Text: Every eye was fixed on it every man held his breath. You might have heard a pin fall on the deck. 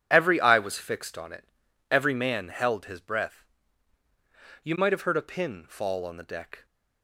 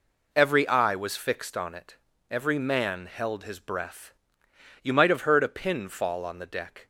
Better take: neither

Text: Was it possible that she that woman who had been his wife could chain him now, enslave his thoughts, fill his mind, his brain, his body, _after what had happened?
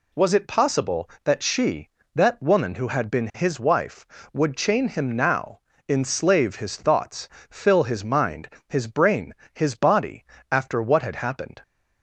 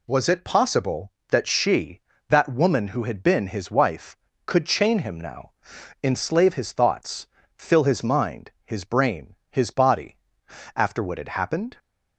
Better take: second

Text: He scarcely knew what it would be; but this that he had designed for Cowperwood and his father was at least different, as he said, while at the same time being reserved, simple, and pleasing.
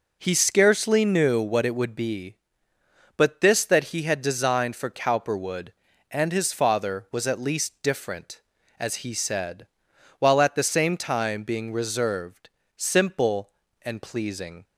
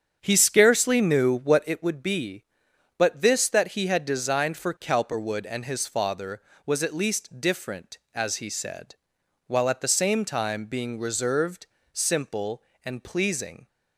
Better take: first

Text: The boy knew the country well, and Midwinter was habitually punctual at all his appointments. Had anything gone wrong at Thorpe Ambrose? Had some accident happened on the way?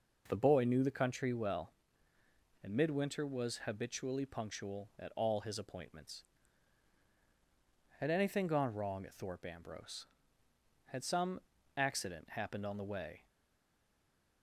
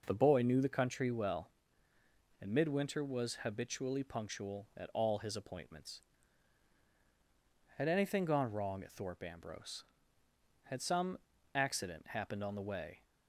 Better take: second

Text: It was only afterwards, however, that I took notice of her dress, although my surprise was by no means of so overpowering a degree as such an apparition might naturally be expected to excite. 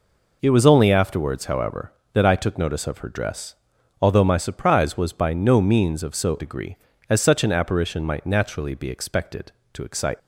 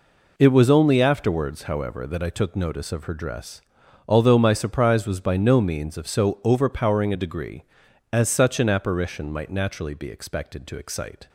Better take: second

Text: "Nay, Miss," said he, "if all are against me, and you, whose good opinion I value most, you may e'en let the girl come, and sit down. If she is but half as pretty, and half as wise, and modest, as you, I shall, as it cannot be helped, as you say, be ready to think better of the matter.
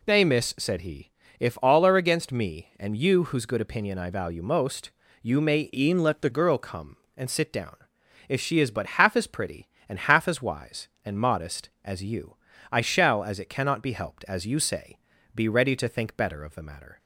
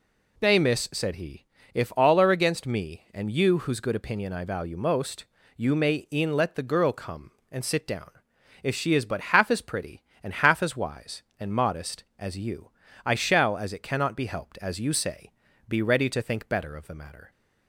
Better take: second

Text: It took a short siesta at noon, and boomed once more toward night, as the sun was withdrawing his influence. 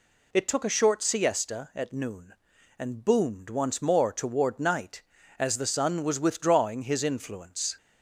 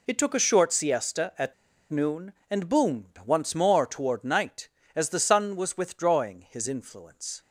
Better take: first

